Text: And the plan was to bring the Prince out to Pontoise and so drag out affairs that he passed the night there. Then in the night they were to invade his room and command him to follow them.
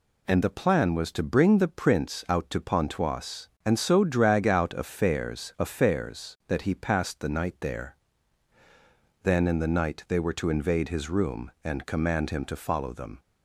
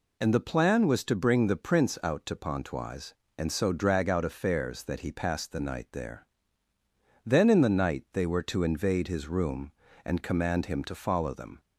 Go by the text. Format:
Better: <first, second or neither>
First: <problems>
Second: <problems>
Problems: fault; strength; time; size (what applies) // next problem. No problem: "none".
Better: second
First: says "affairs" twice; at 5.5 s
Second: none